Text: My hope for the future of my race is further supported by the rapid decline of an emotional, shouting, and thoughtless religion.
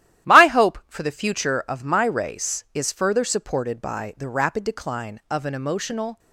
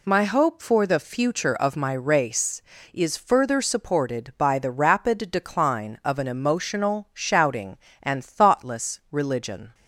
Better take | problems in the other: second | starts louder than the rest; strong; until 1.3 s; 13 dB // stops before "shouting and thoughtless religion"; at 6.1 s

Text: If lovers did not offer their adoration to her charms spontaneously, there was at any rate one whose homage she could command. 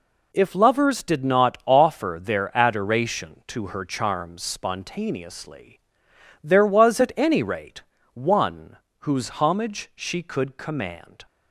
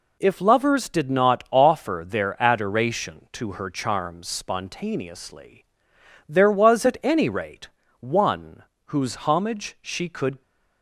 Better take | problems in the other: first | pauses between "rate" and "one"; slight; at 7.6 s; 0.32 s long; slight in the first // pauses between "one" and "whose"; slight; at 8.6 s; 0.22 s long; slight in the first // stops before "command"; at 10.4 s

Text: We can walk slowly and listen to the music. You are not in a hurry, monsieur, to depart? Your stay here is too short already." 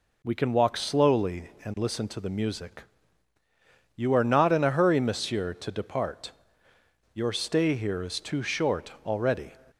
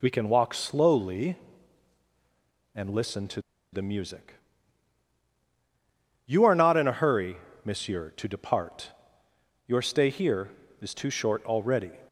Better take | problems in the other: first | pauses between "to" and "the"; slight; at 3.4 s; 0.31 s long

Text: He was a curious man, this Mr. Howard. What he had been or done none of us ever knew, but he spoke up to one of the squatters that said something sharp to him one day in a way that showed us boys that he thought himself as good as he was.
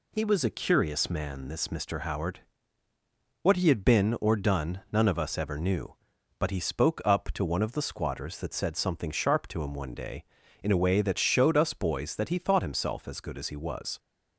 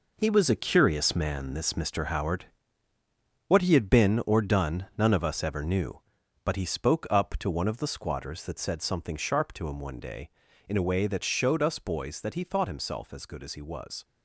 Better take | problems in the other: first | gets quieter; strong; throughout; 8.5 dB

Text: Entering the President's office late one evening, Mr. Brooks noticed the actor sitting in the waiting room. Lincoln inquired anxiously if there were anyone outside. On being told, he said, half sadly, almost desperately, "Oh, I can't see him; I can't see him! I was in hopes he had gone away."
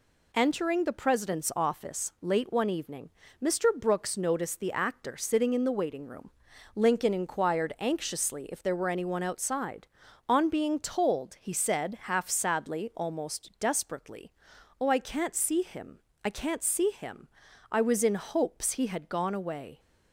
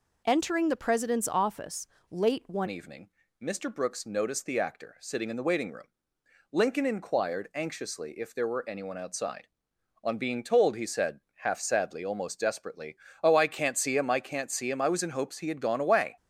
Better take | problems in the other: first | pauses between "office" and "late"; slight; at 1.8 s; 0.24 s long // changes voice at "evening"; from 2.6 s on; 13.5 s long

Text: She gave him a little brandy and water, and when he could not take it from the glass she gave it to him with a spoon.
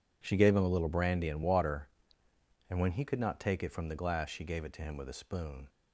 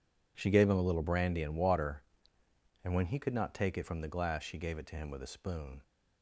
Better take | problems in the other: neither | none

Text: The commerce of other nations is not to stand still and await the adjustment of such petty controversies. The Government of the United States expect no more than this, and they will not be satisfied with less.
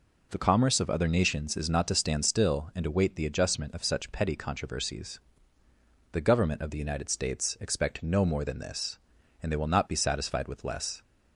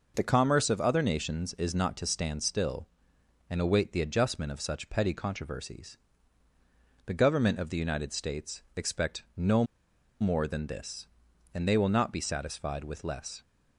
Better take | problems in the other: first | pauses between "no" and "more"; noticeable; at 9.6 s; 0.55 s long

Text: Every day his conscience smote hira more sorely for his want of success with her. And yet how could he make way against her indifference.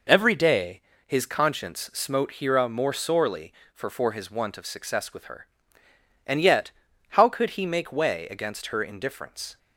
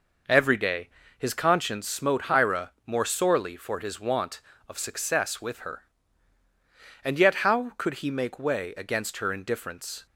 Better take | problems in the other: second | pauses between "day" and "his"; slight; at 0.7 s; 0.26 s long; slight in the second // says "for" twice; at 3.8 s // pauses between "yet" and "how"; at 6.6 s; 0.40 s long

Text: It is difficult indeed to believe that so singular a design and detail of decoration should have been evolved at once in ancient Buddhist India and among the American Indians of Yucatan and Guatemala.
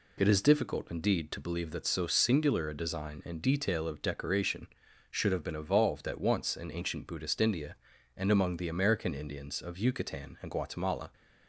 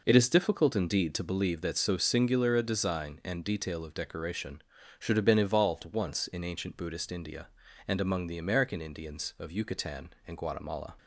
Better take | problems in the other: first | skips "at"; at 5.8 s

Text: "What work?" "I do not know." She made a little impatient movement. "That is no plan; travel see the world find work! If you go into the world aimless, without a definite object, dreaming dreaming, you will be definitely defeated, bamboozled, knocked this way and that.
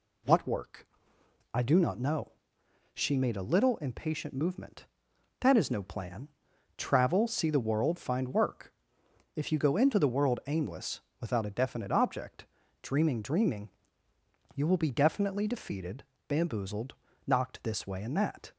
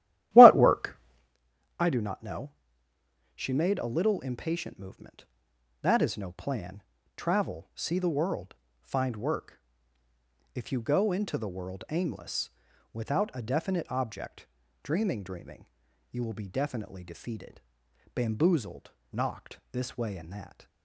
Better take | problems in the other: first | starts louder than the rest; strong; until 1.4 s; 13.5 dB // pauses between "world" and "find"; slight; at 8.5 s; 0.26 s long

